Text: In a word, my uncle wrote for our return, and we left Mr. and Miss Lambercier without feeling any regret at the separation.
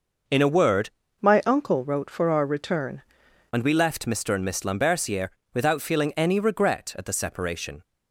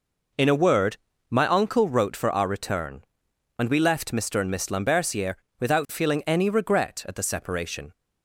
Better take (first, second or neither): second